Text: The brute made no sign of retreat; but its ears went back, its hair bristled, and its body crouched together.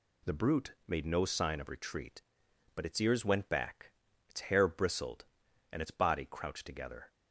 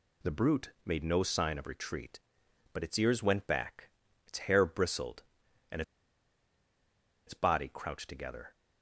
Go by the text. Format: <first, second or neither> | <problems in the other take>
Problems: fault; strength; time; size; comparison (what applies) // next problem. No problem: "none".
first | pauses between "and" and "its"; strong; at 5.8 s; 1.4 s long